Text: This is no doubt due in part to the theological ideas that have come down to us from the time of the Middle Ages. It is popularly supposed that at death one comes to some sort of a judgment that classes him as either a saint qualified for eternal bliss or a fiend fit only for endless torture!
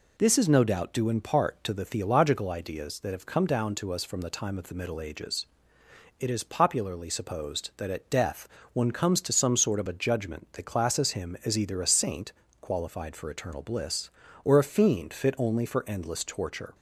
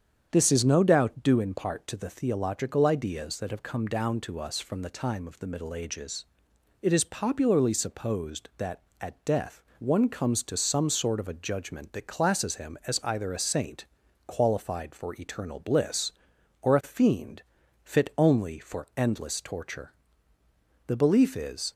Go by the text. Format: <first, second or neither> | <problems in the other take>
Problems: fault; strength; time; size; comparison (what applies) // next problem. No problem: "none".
first | starts louder than the rest; strong; until 1.3 s; 8 dB // pauses between "death" and "one"; slight; at 9.6 s; 0.16 s long; slight in the first // pauses between "saint" and "qualified"; at 13.8 s; 0.40 s long; slight in the first // pauses between "fiend" and "fit"; at 17.4 s; 0.42 s long // goes on to say "The belief is"; noticeable; from 20.8 s on; 0.84 s long